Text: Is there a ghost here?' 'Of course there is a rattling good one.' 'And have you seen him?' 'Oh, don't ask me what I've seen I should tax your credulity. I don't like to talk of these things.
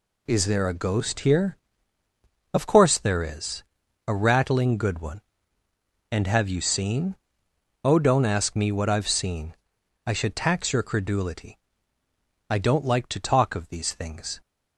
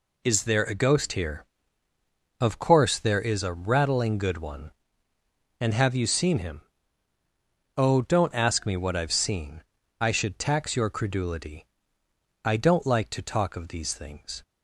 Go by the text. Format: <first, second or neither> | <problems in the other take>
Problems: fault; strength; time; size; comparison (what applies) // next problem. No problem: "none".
second | pauses between "is" and "a"; noticeable; at 3.6 s; 0.46 s long // skips "him"; at 7.4 s // pauses between "seen" and "I"; noticeable; at 9.5 s; 0.50 s long; also in the second